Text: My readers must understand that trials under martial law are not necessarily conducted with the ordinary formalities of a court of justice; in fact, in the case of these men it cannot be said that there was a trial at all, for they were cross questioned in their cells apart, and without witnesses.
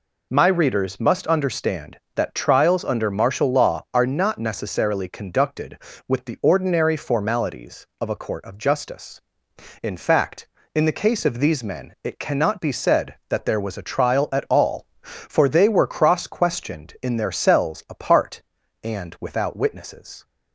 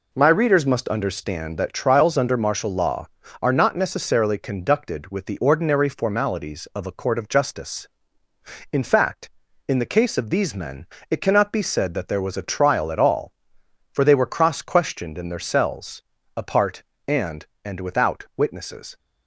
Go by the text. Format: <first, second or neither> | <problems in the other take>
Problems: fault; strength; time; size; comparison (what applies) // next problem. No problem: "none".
first | pauses between "men" and "it"; slight; at 10.8 s; 0.24 s long // pauses between "cells" and "apart"; slight; at 16.0 s; 0.34 s long // says "and" twice; at 17.6 s